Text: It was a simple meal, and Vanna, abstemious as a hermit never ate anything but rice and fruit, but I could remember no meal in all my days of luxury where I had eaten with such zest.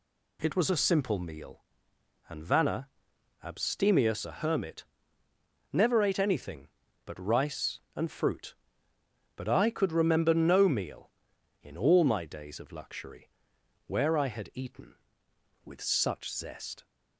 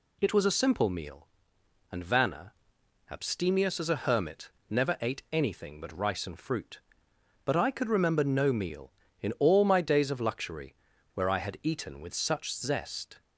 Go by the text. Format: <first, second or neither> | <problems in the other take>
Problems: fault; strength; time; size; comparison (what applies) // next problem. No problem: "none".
second | skips "as"; at 4.2 s // pauses between "hermit" and "never"; noticeable; at 4.8 s; 0.88 s long; slight in the second // pauses between "luxury" and "where"; noticeable; at 13.2 s; 0.58 s long; also in the second